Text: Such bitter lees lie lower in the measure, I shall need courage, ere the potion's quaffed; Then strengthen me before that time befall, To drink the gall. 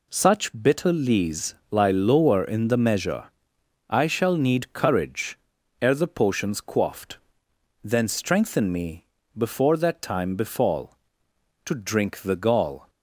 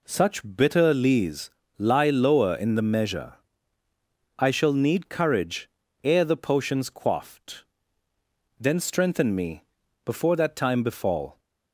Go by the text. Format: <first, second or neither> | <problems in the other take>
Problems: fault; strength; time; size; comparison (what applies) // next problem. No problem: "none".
first | pauses between "lees" and "lie"; slight; at 1.5 s; 0.26 s long; slight in the first // pauses between "me" and "before"; at 9.6 s; 0.40 s long; slight in the first // stops before "To drink the gall"; at 11.3 s